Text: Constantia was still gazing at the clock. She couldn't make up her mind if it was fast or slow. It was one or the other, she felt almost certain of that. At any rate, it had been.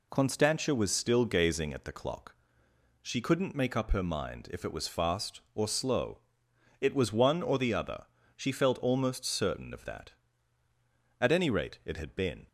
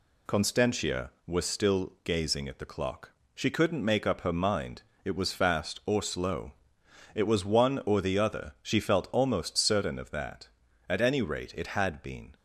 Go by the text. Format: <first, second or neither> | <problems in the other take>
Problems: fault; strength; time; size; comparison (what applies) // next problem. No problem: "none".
first | skips "if"; at 4.9 s